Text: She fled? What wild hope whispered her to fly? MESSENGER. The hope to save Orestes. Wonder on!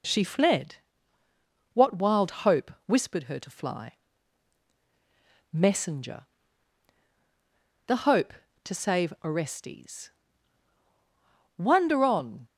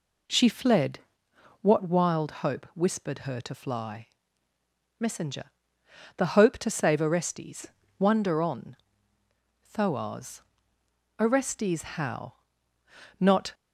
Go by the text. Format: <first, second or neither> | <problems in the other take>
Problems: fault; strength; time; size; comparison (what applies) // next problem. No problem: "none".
first | goes on to say "THOAS Orestes how Not"; strong; from 9.6 s on; 3.8 s long